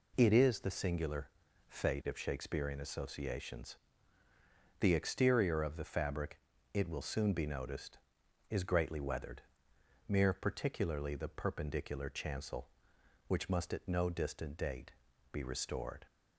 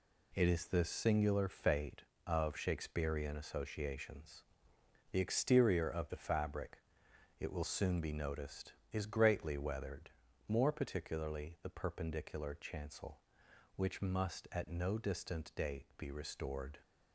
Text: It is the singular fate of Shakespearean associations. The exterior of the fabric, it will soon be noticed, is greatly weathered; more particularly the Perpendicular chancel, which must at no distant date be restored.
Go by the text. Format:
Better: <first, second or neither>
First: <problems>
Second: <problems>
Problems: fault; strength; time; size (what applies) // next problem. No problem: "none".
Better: second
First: pauses between "singular" and "fate"; at 1.2 s; 0.40 s long // says "mere" for "more"; at 10.0 s // pauses between "date" and "be"; at 14.8 s; 0.42 s long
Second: none